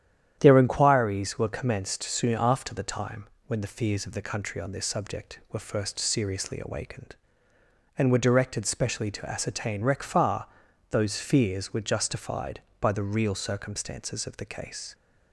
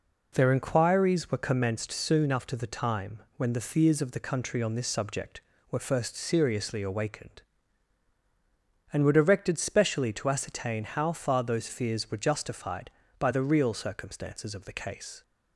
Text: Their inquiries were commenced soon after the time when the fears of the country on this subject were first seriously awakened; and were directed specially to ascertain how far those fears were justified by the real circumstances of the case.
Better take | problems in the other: second | starts louder than the rest; strong; until 1.4 s; 10 dB // pauses between "time" and "when"; slight; at 3.2 s; 0.22 s long; slight in the second // says "rec" for "how"; at 9.8 s // pauses between "far" and "those"; at 10.4 s; 0.42 s long

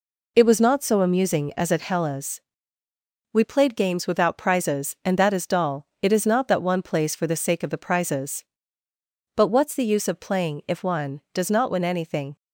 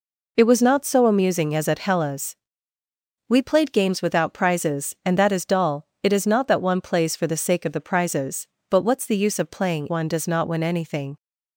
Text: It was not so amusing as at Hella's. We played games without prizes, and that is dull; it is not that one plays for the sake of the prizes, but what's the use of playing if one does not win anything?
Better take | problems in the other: first | skips "if"; at 9.8 s

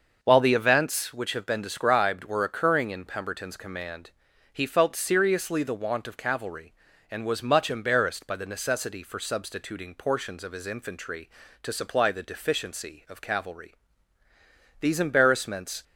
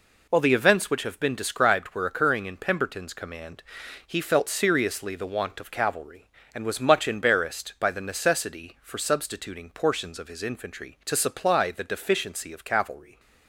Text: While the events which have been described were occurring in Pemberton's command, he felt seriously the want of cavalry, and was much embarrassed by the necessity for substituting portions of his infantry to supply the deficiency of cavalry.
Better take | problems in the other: second | starts louder than the rest; until 1.2 s; 6 dB // goes on to say "These embarrassments"; noticeable; from 14.7 s on; 1.0 s long

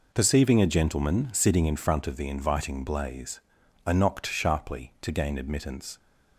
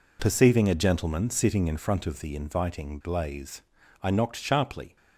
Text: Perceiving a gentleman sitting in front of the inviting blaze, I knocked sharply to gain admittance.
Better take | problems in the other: first | stops before "to gain admittance"; at 4.9 s

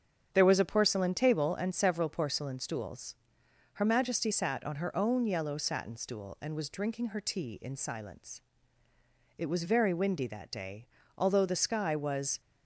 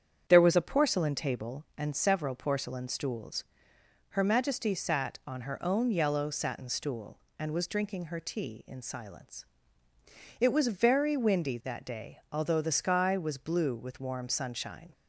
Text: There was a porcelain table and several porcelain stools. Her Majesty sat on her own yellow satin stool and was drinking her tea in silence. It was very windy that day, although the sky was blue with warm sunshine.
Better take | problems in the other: second | starts louder than the rest; strong; until 1.3 s; 7.5 dB; strong in the second // stops before "blue with warm sunshine"; at 12.4 s

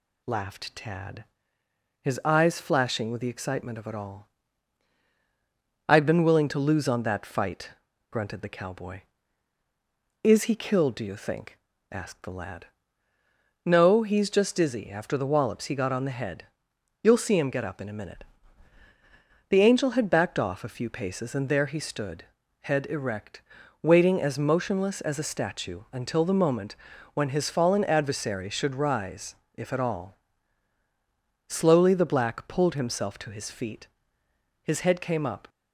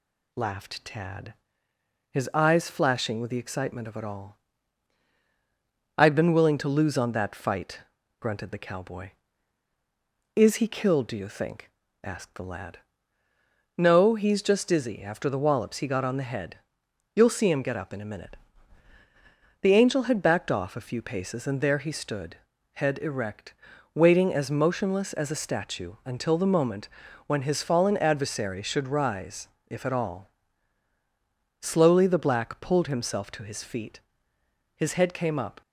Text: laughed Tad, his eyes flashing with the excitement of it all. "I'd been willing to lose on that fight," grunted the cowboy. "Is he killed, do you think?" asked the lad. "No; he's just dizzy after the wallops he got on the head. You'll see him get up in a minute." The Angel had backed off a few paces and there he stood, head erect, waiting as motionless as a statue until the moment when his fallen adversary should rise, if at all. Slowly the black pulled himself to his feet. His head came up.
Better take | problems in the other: neither | pauses between "moment" and "when"; the same in both

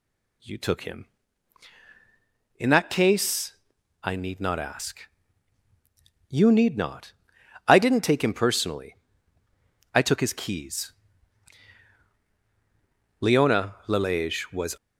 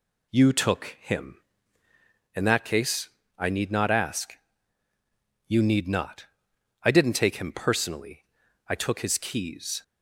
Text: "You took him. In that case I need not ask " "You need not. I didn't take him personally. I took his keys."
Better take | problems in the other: second | pauses between "case" and "I"; noticeable; at 3.5 s; 0.46 s long; slight in the second // goes on to say "Leona Lalage was"; from 13.1 s on; 1.5 s long

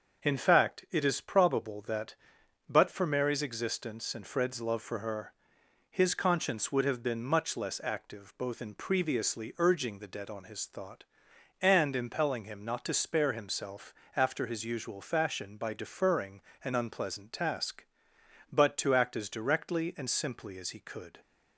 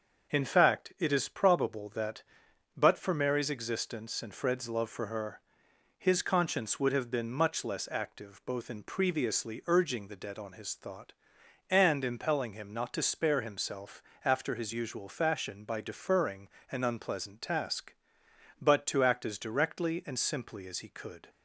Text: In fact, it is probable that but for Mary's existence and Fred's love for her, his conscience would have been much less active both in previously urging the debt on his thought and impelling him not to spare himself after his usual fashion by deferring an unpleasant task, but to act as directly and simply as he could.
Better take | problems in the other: neither | starts louder than the rest; the same in both // pauses between "himself" and "after"; slight; the same in both // pauses between "deferring" and "an"; slight; the same in both

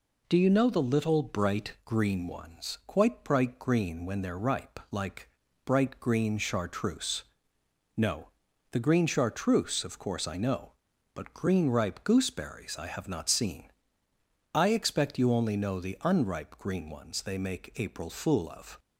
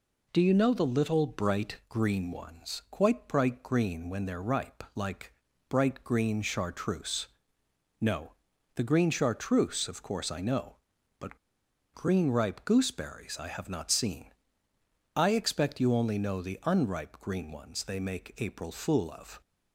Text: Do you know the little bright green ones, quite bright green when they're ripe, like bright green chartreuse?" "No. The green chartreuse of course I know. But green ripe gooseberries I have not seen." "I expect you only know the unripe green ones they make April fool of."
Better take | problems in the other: first | pauses between "like" and "bright"; at 5.3 s; 0.38 s long; also in the first // pauses between "But" and "green"; noticeable; at 11.3 s; 0.56 s long

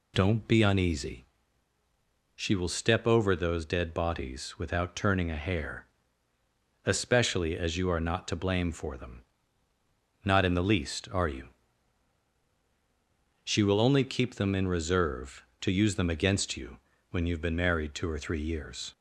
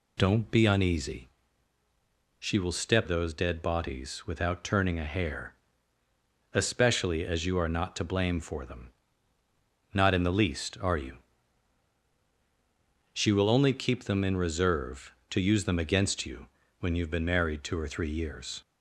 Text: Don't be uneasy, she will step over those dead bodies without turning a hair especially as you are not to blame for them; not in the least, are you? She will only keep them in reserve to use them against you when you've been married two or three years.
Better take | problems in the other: first | skips "over"; at 3.0 s // pauses between "hair" and "especially"; at 5.5 s; 1.0 s long; also in the first // pauses between "you" and "when"; slight; at 16.4 s; 0.34 s long; slight in the first

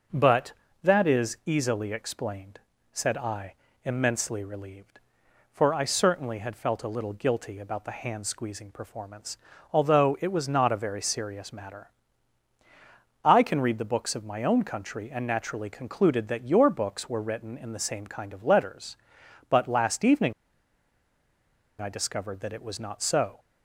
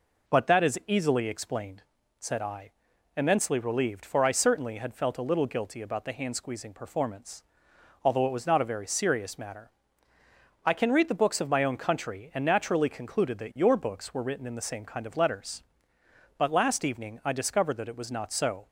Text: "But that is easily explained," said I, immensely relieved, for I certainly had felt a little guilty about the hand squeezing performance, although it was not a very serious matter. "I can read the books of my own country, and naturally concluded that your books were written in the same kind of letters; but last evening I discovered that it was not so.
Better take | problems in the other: second | pauses between "evening" and "I"; strong; at 20.3 s; 1.4 s long

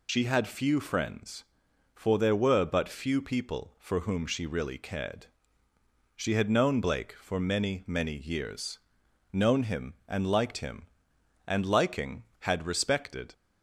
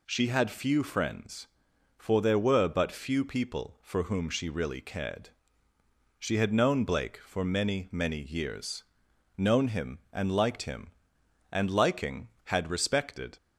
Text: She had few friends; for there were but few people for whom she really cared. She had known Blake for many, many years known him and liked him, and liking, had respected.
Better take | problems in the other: second | loses the start of "She"; at 0.0 s; 65 ms // pauses between "years" and "known"; noticeable; at 8.7 s; 0.54 s long; noticeable in the second

